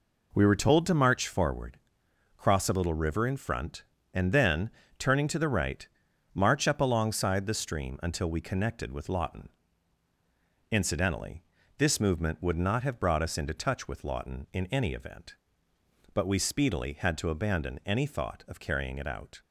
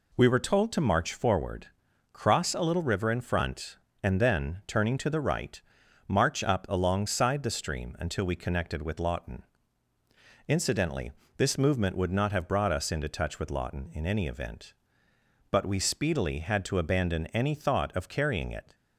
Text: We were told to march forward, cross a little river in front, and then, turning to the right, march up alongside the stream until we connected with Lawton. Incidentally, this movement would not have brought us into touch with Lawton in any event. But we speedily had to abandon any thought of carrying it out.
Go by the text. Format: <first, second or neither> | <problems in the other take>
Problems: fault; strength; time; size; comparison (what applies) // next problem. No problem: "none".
first | stops before "out"; at 18.7 s